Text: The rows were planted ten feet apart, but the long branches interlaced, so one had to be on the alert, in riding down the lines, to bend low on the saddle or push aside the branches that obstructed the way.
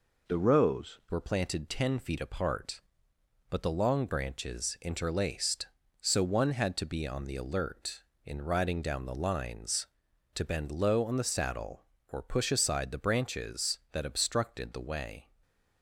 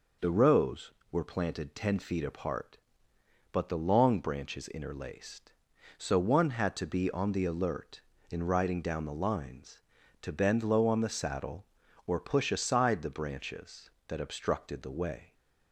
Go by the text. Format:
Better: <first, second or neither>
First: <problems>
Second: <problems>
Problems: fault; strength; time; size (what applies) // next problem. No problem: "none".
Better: second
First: changes voice at "were"; from 1.1 s on; 14.2 s long // stays silent after the last word; slight; from 15.2 s on; 0.6 s long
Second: none